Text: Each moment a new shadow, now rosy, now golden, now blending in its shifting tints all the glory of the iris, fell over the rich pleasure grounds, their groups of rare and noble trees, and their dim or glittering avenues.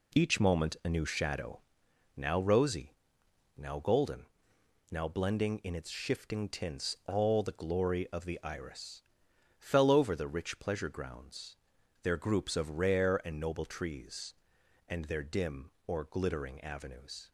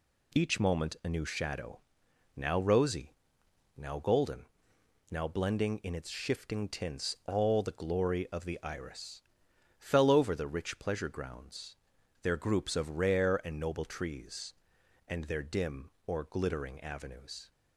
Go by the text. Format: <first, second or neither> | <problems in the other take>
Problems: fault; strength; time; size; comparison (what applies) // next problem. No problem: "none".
second | starts louder than the rest; slight; until 1.9 s; 2.5 dB